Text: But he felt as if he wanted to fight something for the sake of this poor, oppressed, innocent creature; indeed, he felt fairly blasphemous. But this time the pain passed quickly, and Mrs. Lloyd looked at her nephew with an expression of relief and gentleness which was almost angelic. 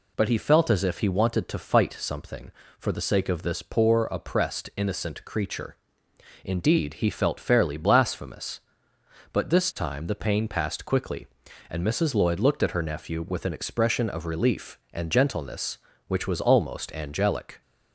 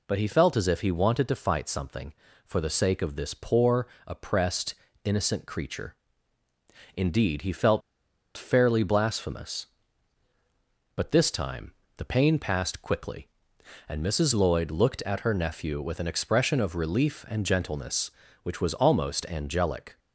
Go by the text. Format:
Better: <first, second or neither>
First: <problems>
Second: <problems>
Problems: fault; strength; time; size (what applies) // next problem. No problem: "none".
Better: first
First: none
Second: pauses between "felt" and "fairly"; noticeable; at 7.8 s; 0.55 s long // pauses between "time" and "the"; slight; at 11.7 s; 0.24 s long